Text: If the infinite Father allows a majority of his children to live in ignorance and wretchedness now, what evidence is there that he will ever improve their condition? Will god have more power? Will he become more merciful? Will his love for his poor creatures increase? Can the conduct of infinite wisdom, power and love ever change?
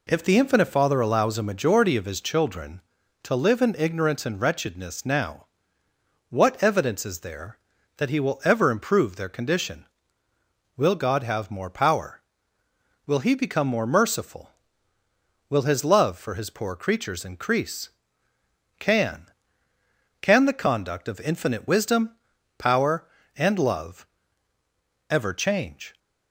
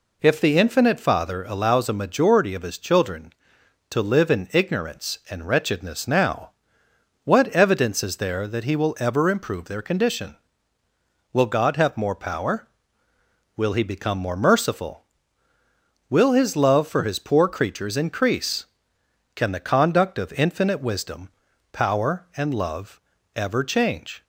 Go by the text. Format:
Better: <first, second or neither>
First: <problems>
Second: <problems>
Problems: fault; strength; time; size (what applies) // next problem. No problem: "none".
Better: second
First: says "Can" twice; at 20.2 s // pauses between "love" and "ever"; at 24.0 s; 1.0 s long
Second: pauses between "love" and "ever"; slight; at 22.9 s; 0.36 s long